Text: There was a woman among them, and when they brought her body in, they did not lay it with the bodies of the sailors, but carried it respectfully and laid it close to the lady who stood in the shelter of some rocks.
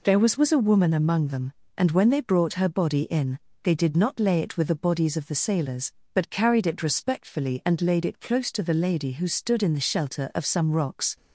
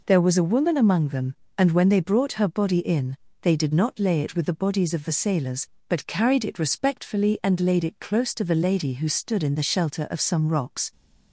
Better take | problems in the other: second | says "was" twice; at 0.3 s

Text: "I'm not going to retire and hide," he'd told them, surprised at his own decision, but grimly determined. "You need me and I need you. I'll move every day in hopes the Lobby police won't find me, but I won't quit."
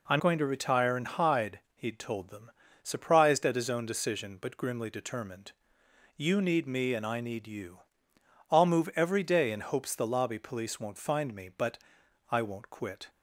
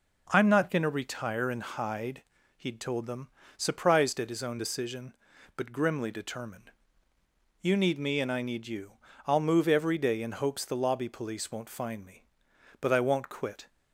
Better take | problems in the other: second | skips "not"; at 0.2 s // pauses between "but" and "I"; noticeable; at 11.7 s; 0.54 s long

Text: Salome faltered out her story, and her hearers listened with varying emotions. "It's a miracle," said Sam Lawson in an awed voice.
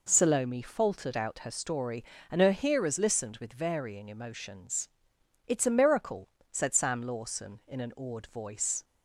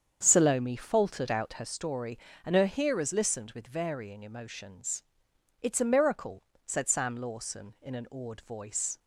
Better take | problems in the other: first | starts louder than the rest; strong; until 1.7 s; 7.5 dB

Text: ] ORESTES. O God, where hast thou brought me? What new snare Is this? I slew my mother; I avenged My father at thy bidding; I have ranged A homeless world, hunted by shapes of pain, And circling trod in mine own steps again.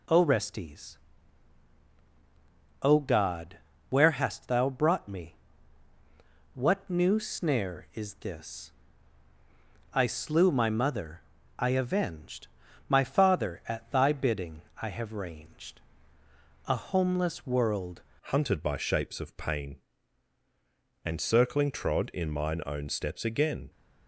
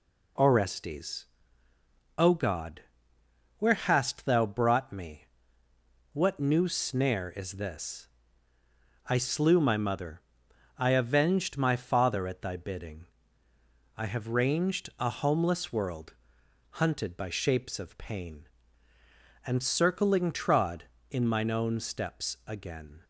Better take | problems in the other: second | pauses between "avenged" and "My"; at 12.4 s; 0.38 s long // pauses between "ranged" and "A"; noticeable; at 15.8 s; 0.88 s long // changes voice at "hunted"; from 18.3 s on; 5.3 s long

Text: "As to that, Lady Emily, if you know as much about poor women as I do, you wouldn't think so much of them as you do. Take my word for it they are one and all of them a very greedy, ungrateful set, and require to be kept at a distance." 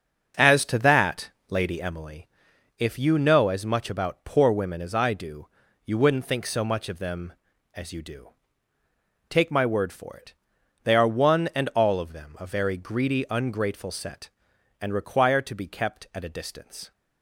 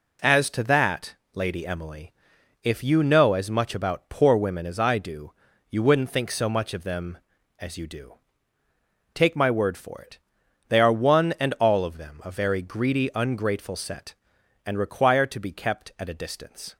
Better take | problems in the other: second | starts louder than the rest; until 1.9 s; 6.5 dB // pauses between "it" and "they"; noticeable; at 10.3 s; 0.50 s long; noticeable in the second

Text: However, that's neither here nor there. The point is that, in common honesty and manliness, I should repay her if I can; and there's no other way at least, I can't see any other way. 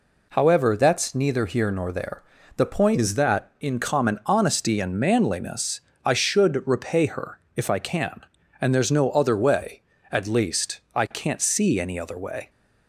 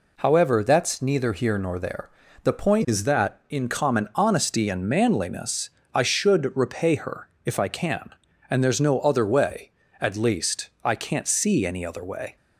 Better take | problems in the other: neither | pauses between "her" and "if"; slight; the same in both

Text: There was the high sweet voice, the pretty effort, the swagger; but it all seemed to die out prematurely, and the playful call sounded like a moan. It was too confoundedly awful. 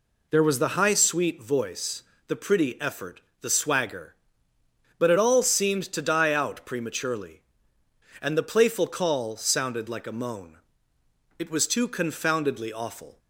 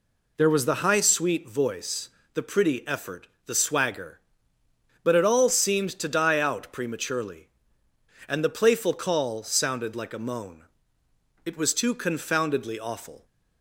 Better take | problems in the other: neither | none

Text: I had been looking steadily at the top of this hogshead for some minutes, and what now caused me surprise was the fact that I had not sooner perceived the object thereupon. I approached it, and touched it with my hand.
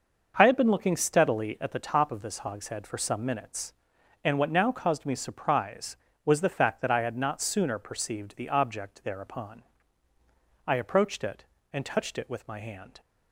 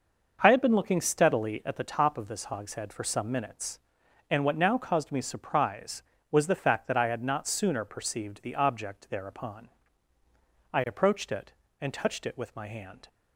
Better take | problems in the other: neither | starts louder than the rest; noticeable; the same in both

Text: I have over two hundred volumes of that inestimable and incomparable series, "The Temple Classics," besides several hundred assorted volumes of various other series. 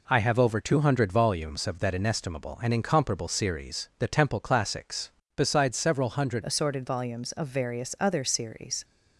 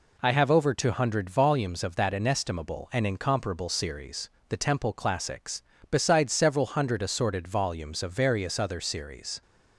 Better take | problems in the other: second | changes voice at "assorted"; from 6.4 s on; 2.4 s long

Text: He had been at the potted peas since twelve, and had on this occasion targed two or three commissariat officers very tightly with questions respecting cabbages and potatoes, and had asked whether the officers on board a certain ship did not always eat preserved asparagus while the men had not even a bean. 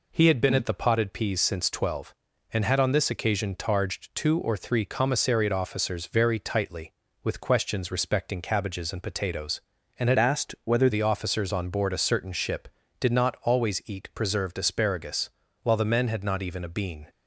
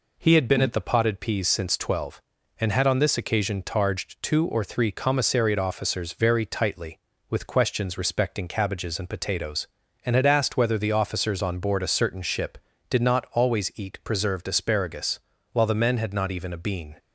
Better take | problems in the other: second | changes voice from "asked" to "whether"; from 10.1 to 10.8 s; 0.7 s long // pauses between "asparagus" and "while"; slight; at 15.2 s; 0.32 s long; slight in the second

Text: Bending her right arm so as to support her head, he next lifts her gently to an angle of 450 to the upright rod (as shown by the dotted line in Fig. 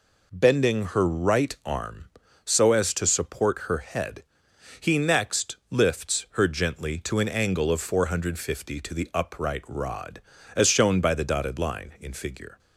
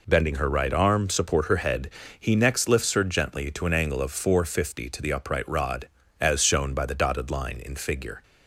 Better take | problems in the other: first | skips "so as to"; at 1.0 s

